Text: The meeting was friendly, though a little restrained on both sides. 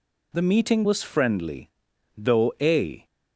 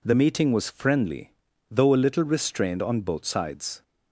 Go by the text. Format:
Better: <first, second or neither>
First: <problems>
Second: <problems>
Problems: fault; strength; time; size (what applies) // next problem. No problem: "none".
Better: second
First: stops before "little restrained on both sides"; at 3.0 s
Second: none